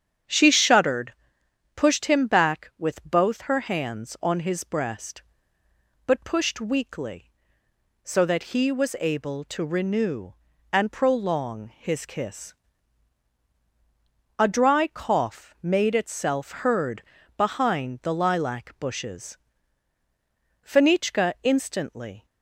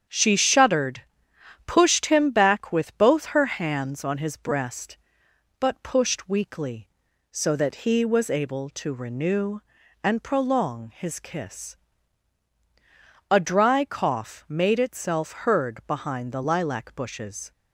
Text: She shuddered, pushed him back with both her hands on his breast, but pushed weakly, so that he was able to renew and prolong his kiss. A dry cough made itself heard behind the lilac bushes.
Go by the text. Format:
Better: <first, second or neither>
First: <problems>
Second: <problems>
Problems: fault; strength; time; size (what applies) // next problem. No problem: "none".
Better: second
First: starts louder than the rest; strong; until 1.8 s; 8.5 dB // pauses between "heard" and "behind"; slight; at 17.0 s; 0.34 s long // goes on to say "Fenichka instantly"; from 20.6 s on; 1.6 s long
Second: starts louder than the rest; strong; until 1.7 s; 8 dB